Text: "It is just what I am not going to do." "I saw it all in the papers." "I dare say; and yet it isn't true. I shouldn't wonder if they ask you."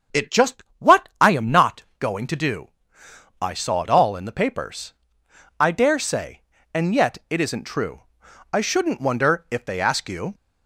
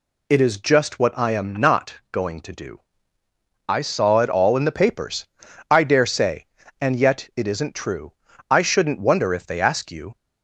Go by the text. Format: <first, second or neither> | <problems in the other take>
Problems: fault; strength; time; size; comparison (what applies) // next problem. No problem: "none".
second | starts louder than the rest; strong; until 1.4 s; 7 dB // skips "is"; at 0.3 s // pauses between "just" and "what"; slight; at 0.6 s; 0.18 s long // pauses between "not" and "going"; slight; at 1.8 s; 0.16 s long; slight in the second